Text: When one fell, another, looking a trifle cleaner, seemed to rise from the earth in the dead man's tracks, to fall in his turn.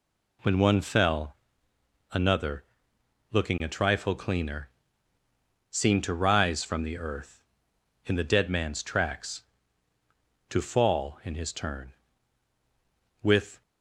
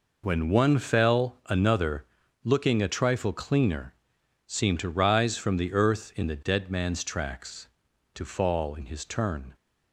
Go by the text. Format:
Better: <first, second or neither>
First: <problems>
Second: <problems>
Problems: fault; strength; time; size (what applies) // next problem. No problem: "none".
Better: second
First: goes on to say "With"; slight; from 13.2 s on; 0.40 s long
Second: none